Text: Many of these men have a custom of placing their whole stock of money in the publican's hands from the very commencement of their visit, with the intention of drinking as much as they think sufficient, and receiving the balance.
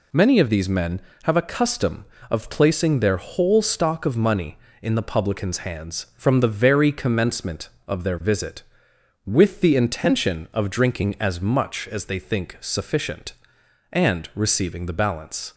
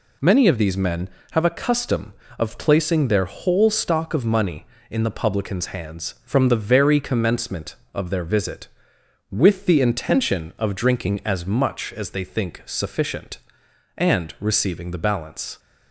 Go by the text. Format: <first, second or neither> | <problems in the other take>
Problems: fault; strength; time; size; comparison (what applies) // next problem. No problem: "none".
neither | none